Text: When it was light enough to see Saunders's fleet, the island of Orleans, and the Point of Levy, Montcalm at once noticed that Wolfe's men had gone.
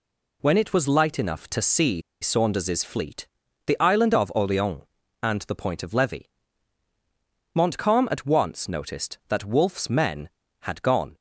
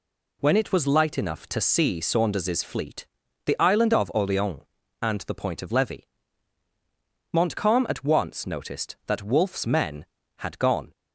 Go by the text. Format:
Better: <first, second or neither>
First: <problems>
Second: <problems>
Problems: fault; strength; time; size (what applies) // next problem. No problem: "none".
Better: second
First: pauses between "see" and "Saunders's"; slight; at 2.0 s; 0.20 s long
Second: none